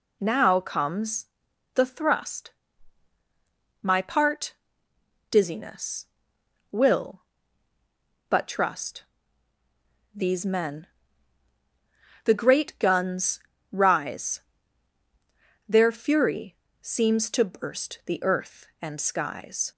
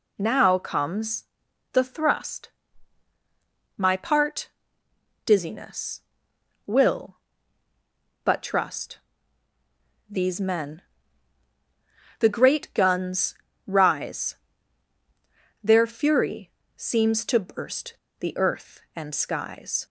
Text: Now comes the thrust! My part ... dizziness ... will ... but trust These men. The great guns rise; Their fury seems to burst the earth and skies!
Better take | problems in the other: first | pauses between "comes" and "the"; noticeable; at 1.2 s; 0.48 s long; noticeable in the first // pauses between "trust" and "These"; at 8.9 s; 1.1 s long; also in the first // pauses between "guns" and "rise"; slight; at 13.3 s; 0.32 s long; slight in the first // pauses between "fury" and "seems"; slight; at 16.5 s; 0.24 s long; slight in the first // pauses between "burst" and "the"; slight; at 17.9 s; 0.23 s long

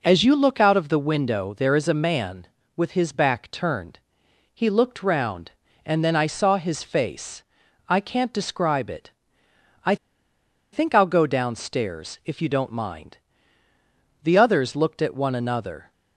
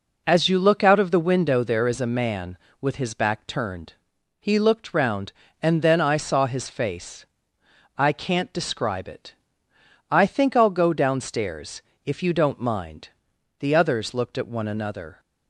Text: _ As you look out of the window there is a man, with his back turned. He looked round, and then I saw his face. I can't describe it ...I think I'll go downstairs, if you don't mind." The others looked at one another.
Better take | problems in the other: second | pauses between "I" and "think"; noticeable; at 9.9 s; 0.77 s long

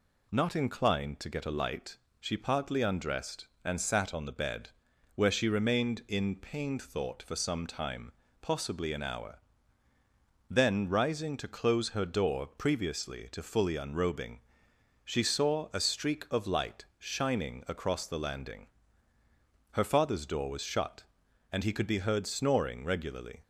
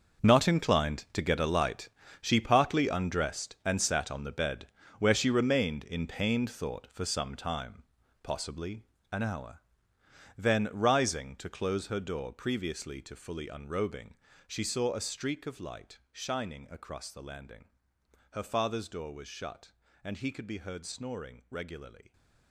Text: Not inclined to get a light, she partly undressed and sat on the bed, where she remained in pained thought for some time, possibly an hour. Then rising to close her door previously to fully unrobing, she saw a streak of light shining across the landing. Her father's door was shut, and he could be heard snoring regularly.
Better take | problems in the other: first | gets quieter; strong; throughout; 13.5 dB // pauses between "possibly" and "an"; slight; at 8.8 s; 0.26 s long

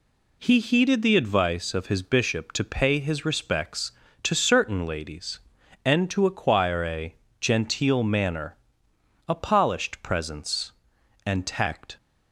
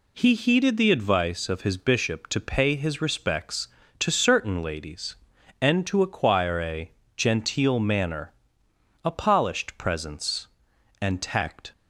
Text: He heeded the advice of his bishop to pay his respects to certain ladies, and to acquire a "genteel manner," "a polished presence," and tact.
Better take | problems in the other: neither | pauses between "a" and "genteel"; slight; the same in both

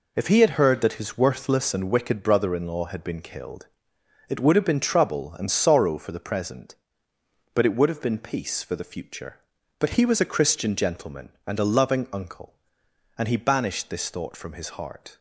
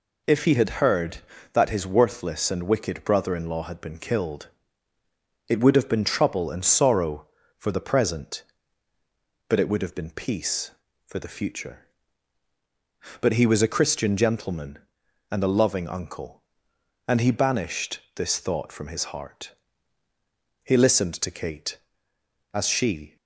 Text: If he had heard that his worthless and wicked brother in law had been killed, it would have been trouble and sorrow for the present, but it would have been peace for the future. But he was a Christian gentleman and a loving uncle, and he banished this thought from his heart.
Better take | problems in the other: first | pauses between "banished" and "this"; slight; at 17.9 s; 0.16 s long // goes on to say "He listened to Kate as she"; strong; from 20.6 s on; 2.5 s long

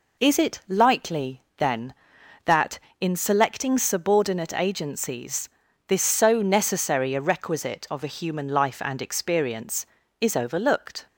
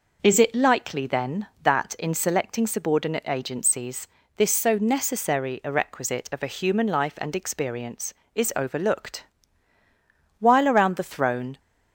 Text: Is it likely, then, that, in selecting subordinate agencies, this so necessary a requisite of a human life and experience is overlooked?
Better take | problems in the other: first | goes on to say "While around the throne"; noticeable; from 10.4 s on; 1.1 s long

